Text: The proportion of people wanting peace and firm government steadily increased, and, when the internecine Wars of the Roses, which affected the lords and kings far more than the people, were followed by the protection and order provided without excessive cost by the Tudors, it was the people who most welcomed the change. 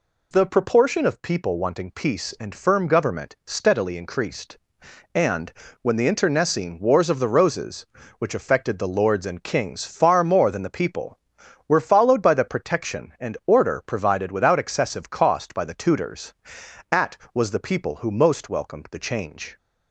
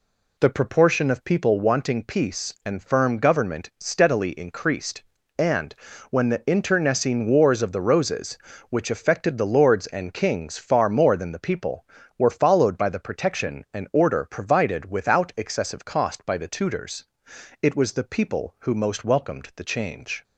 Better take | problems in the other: second | says "at" for "it"; at 16.9 s

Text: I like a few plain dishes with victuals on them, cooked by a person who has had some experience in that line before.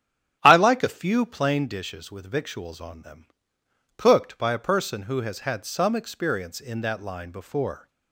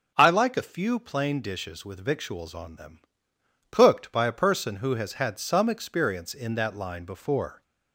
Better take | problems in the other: second | starts louder than the rest; strong; until 1.8 s; 9.5 dB

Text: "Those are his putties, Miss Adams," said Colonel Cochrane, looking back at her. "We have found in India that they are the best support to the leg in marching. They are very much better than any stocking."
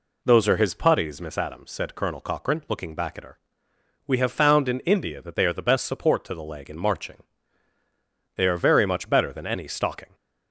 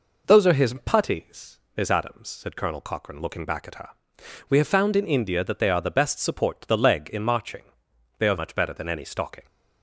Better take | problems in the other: first | skips "very"; at 8.3 s

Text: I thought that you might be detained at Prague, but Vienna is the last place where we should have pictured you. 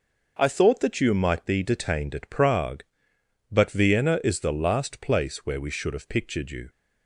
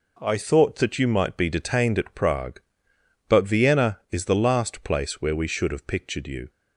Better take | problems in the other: neither | none

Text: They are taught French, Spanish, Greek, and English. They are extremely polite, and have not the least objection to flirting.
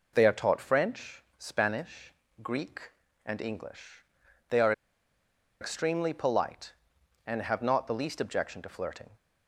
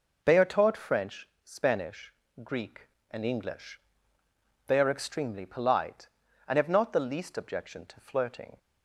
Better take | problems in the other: second | pauses between "are" and "extremely"; noticeable; at 4.7 s; 0.88 s long

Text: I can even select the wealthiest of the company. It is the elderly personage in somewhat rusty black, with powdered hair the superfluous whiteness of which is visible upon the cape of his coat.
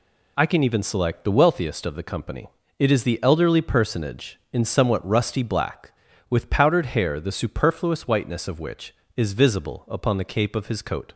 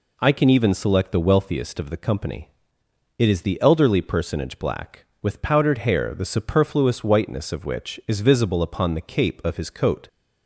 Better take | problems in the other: first | skips "in somewhat rusty"; at 4.5 s

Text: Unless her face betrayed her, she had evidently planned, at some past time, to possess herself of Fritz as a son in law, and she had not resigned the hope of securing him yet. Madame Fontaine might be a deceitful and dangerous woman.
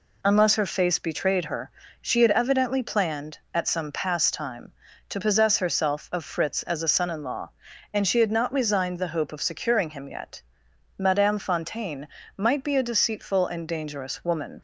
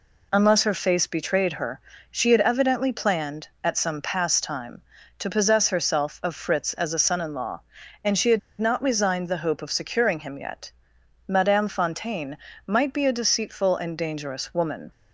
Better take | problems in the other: first | pauses between "had" and "not"; slight; at 8.3 s; 0.20 s long // pauses between "Fontaine" and "might"; slight; at 12.3 s; 0.28 s long; slight in the first

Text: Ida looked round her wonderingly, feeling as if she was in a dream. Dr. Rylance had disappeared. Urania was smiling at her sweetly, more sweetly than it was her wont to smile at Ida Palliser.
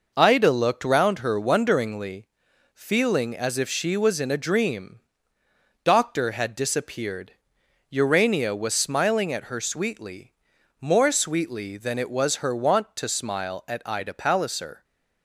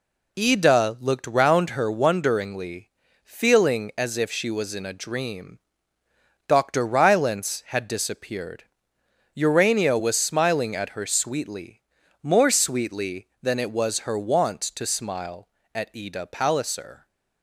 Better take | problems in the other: second | skips "Rylance"; at 6.3 s

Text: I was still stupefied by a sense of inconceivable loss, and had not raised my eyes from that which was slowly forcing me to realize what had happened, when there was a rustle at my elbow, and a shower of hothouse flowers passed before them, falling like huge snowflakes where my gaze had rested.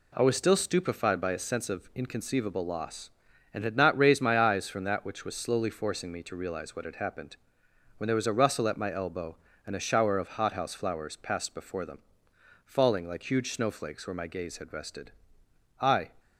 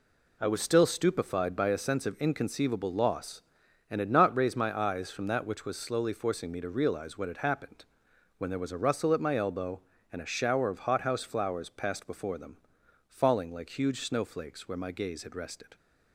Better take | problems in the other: second | goes on to say "I"; slight; from 15.8 s on; 0.32 s long

